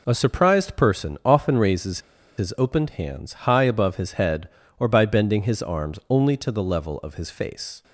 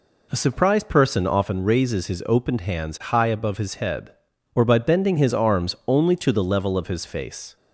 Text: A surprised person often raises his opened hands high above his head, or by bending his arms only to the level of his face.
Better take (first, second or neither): second